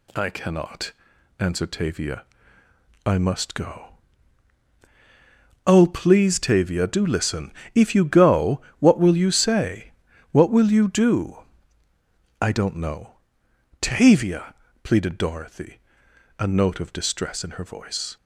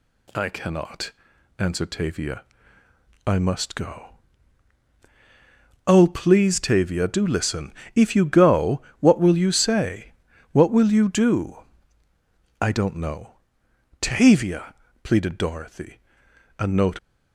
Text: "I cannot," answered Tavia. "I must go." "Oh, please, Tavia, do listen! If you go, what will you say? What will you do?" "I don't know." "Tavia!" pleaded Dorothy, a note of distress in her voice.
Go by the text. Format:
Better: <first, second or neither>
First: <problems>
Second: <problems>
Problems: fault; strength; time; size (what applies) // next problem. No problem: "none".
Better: first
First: none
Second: stops before "of distress in her voice"; at 16.9 s